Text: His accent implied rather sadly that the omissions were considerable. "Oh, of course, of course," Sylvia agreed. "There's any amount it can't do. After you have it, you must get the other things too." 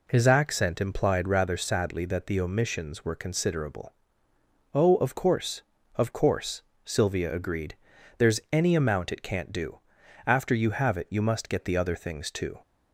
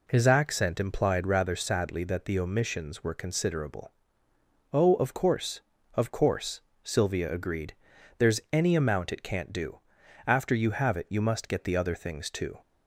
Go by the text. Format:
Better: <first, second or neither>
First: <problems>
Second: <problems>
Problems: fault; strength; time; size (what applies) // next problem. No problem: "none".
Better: neither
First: none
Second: none